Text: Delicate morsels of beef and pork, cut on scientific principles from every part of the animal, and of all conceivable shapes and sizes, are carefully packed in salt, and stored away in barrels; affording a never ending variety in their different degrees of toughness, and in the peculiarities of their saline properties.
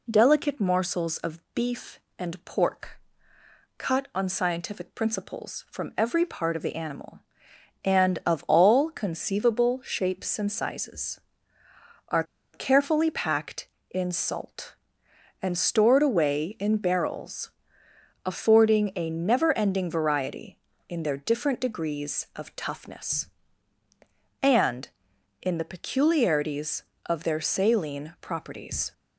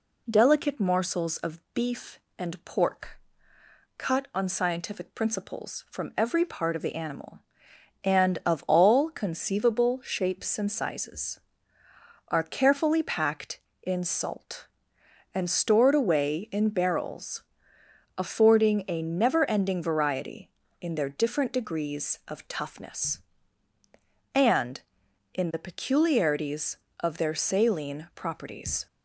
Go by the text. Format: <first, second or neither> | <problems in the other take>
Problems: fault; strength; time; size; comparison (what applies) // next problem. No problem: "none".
second | pauses between "are" and "carefully"; slight; at 12.2 s; 0.30 s long